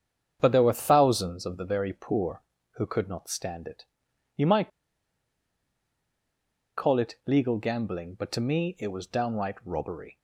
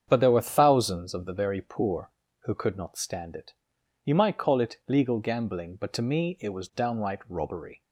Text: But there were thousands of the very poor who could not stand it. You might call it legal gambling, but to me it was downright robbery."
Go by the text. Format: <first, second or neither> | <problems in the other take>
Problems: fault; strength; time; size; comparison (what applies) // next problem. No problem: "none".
second | starts louder than the rest; strong; until 1.4 s; 8 dB; strong in the second // pauses between "might" and "call"; strong; at 4.7 s; 2.0 s long